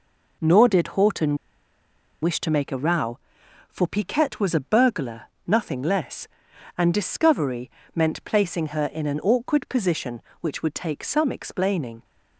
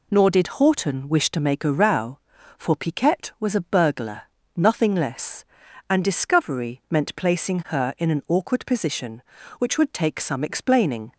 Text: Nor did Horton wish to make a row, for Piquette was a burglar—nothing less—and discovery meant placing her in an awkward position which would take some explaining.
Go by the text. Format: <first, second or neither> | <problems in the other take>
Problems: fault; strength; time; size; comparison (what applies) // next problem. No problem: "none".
second | pauses between "Horton" and "wish"; noticeable; at 1.3 s; 0.87 s long // pauses between "discovery" and "meant"; slight; at 7.6 s; 0.26 s long